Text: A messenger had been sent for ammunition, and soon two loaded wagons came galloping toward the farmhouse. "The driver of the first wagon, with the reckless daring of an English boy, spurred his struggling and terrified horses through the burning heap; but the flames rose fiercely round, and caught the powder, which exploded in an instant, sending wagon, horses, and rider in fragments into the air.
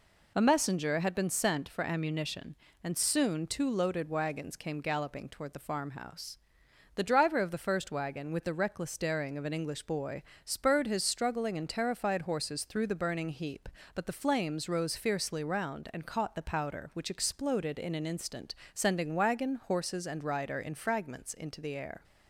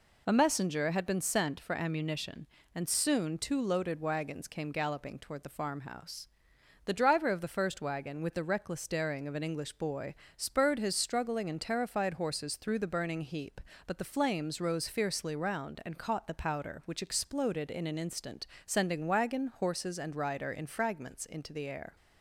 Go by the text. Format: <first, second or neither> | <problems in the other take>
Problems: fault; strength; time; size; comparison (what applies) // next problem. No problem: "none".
neither | none